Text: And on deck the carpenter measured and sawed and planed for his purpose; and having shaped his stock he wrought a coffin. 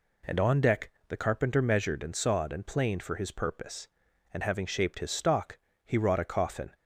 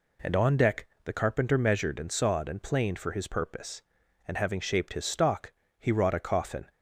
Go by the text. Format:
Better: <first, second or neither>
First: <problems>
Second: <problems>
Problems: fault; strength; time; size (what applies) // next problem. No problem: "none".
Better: neither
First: pauses between "deck" and "the"; slight; at 0.9 s; 0.18 s long // pauses between "stock" and "he"; slight; at 5.5 s; 0.26 s long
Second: pauses between "deck" and "the"; slight; at 0.8 s; 0.18 s long // pauses between "stock" and "he"; slight; at 5.5 s; 0.26 s long